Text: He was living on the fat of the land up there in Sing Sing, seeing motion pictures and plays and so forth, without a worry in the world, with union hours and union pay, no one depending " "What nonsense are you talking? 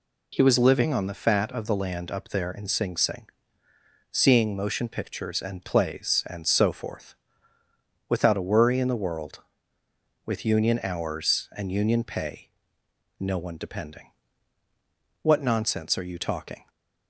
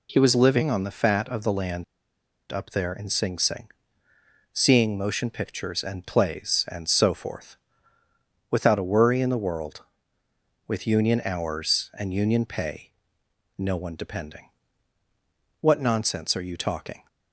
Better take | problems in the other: first | pauses between "land" and "up"; noticeable; at 1.8 s; 0.66 s long

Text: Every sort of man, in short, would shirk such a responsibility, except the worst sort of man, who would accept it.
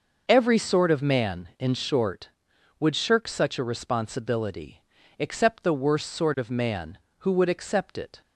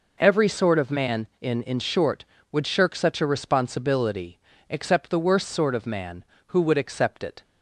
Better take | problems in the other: first | says "in" twice; at 1.6 s

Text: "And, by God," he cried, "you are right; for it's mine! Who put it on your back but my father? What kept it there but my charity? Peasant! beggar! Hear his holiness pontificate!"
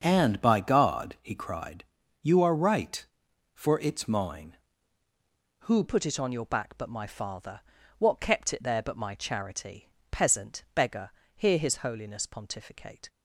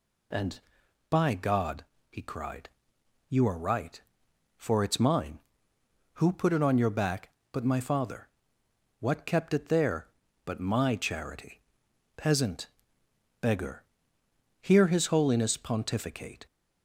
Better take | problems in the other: second | starts louder than the rest; until 1.0 s; 7 dB // changes voice at "put"; from 5.8 s on; 7.2 s long

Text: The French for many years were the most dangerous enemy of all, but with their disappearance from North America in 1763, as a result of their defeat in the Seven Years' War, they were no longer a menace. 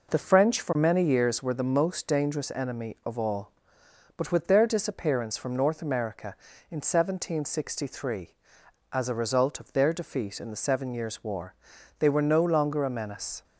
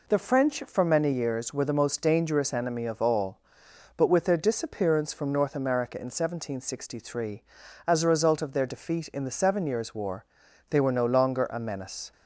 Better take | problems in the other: neither | none

